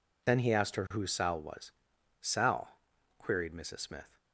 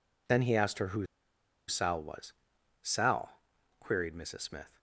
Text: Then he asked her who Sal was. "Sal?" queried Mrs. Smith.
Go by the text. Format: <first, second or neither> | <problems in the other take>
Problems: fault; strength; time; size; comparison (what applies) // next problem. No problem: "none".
first | pauses between "who" and "Sal"; noticeable; at 1.0 s; 0.61 s long